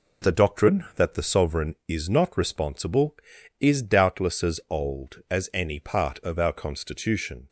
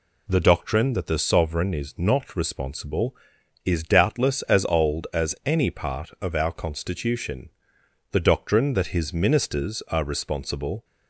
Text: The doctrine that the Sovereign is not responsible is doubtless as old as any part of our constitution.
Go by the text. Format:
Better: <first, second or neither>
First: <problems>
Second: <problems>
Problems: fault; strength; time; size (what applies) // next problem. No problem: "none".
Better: first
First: none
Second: goes on to say "The doctrine that his ministers are responsible"; strong; from 8.1 s on; 2.7 s long